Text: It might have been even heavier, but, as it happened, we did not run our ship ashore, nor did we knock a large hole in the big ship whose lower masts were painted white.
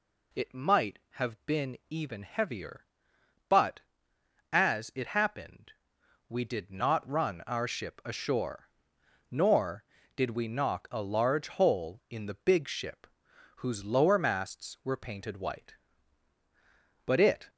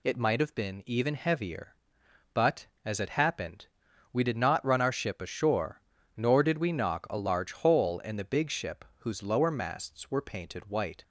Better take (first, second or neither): second